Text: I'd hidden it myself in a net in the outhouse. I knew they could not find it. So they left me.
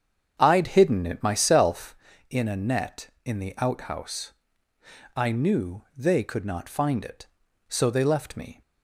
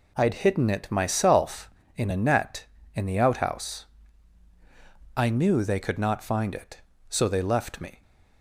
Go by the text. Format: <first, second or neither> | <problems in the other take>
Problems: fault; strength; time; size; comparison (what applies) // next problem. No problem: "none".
second | starts louder than the rest; strong; until 2.0 s; 7.5 dB